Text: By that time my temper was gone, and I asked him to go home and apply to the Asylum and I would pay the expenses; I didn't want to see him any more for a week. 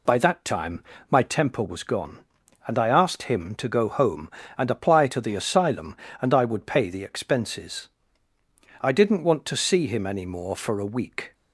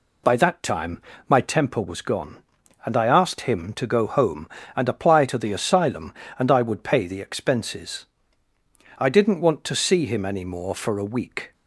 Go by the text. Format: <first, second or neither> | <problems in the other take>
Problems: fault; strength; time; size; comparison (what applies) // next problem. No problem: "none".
neither | pauses between "time" and "my"; slight; the same in both